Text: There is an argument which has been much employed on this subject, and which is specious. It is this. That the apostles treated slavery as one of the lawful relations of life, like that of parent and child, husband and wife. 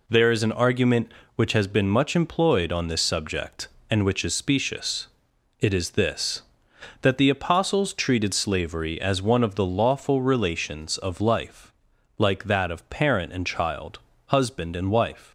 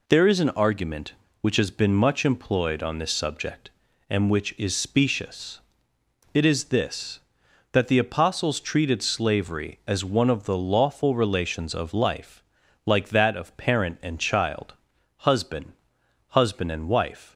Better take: first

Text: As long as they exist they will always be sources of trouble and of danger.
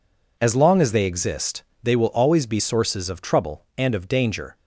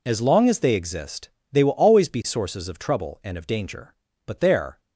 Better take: first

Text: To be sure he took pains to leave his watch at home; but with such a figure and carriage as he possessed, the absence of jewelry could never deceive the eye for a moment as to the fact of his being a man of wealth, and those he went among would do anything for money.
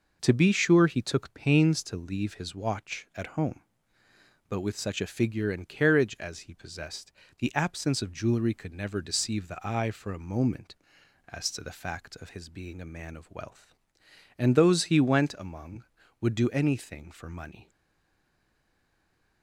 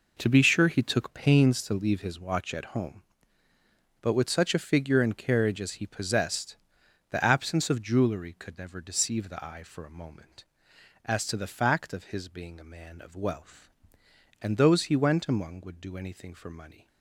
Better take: second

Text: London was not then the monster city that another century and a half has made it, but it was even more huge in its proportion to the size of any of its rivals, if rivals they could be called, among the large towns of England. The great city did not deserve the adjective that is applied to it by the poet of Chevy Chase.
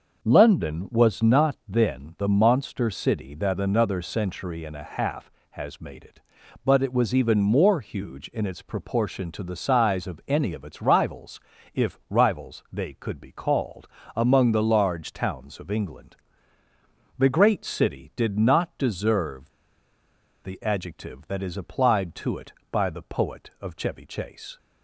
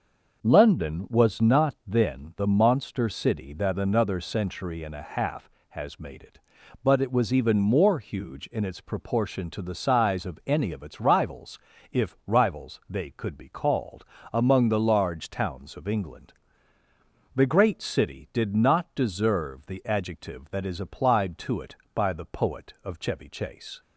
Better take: second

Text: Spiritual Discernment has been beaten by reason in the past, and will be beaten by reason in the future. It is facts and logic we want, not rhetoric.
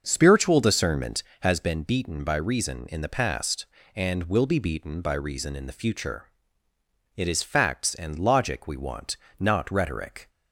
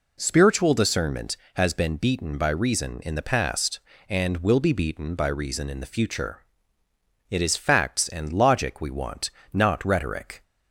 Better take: second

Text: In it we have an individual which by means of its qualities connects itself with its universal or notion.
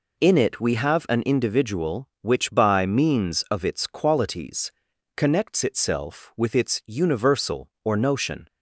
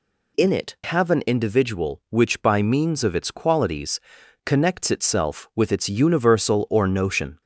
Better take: first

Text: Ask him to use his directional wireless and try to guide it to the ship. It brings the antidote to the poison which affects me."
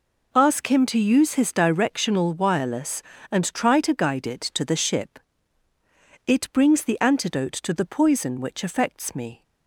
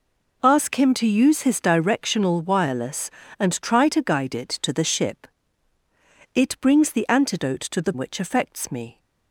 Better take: first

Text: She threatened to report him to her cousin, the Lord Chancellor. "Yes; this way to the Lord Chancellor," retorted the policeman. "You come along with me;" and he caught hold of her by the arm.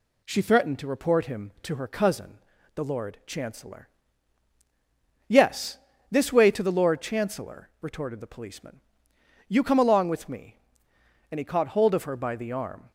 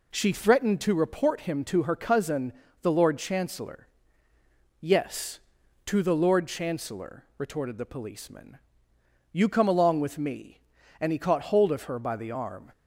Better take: first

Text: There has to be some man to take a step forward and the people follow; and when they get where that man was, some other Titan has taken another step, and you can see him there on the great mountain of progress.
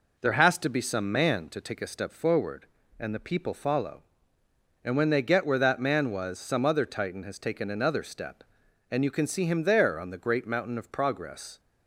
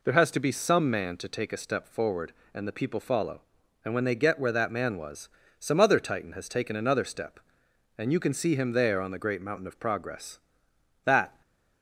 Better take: first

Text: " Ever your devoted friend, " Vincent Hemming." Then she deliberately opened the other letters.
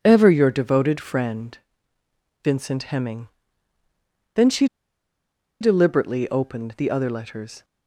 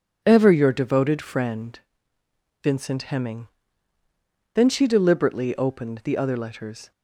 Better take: second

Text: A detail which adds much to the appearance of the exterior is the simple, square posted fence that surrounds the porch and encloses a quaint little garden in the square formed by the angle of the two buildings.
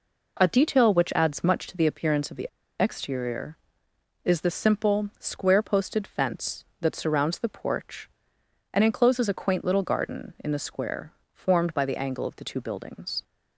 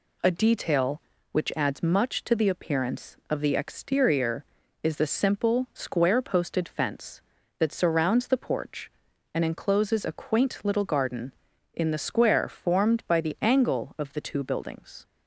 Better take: second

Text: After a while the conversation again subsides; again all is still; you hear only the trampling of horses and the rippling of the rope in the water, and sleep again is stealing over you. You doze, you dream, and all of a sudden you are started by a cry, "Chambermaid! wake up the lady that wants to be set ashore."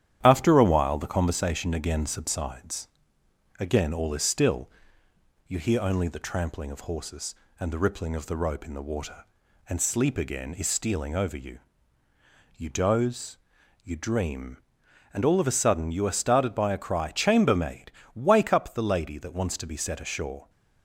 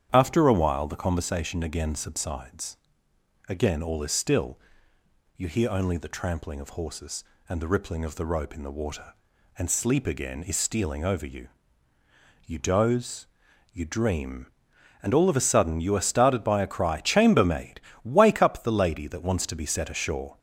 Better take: second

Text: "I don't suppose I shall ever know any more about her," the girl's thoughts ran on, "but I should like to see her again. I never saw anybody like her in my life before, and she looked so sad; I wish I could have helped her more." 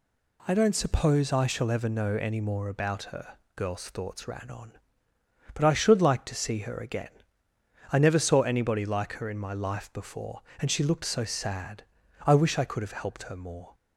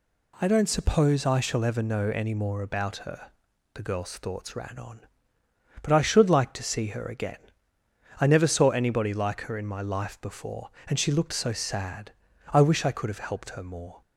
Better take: second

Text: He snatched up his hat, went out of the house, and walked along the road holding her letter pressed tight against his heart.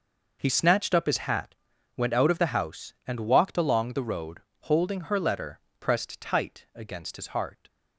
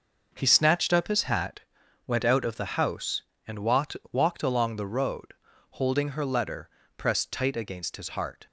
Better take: first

